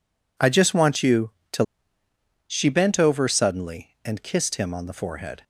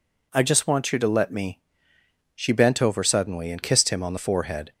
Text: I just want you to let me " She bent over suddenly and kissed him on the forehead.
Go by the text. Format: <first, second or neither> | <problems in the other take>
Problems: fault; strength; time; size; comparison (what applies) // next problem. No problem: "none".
second | skips "let me"; at 1.7 s